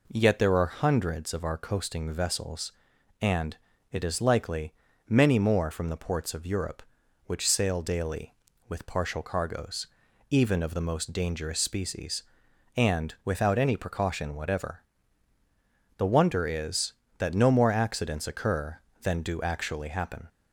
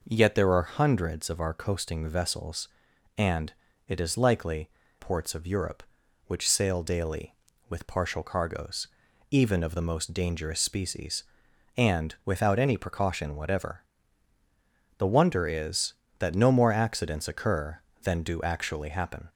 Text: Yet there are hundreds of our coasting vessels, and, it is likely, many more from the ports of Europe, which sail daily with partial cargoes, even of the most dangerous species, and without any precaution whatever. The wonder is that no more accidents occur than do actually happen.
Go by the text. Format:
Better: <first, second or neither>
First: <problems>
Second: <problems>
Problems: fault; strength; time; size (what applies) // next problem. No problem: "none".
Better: first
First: none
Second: skips "many more from the"; at 4.8 s